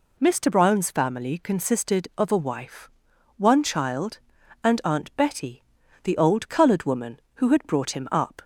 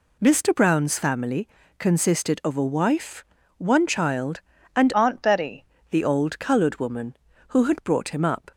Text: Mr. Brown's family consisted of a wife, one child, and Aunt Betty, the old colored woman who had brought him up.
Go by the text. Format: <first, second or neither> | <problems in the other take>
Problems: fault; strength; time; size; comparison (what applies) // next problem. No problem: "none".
first | pauses between "family" and "consisted"; slight; at 1.4 s; 0.30 s long // changes voice from "Aunt" to "Betty"; from 4.9 to 5.6 s; 0.7 s long